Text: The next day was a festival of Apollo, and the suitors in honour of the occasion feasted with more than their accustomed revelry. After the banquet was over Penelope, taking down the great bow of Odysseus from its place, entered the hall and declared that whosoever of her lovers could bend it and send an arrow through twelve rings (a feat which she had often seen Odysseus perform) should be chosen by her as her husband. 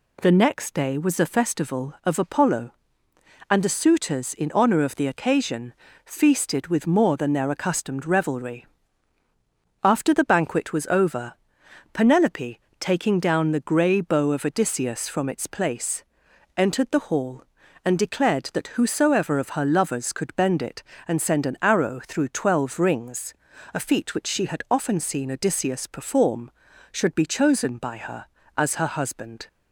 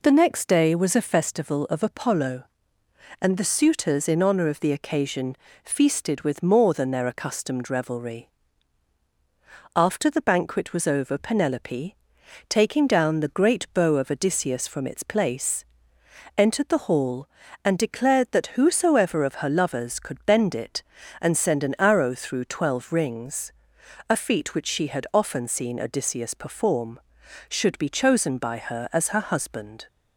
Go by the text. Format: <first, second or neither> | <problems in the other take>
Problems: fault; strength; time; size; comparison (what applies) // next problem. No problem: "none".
second | pauses between "occasion" and "feasted"; slight; at 5.7 s; 0.32 s long; slight in the second // pauses between "over" and "Penelope"; noticeable; at 11.3 s; 0.58 s long // says "grey" for "great"; at 13.6 s